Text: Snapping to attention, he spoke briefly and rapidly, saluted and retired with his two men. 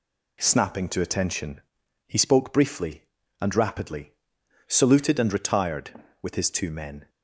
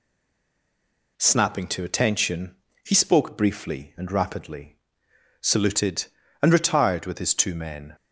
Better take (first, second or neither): first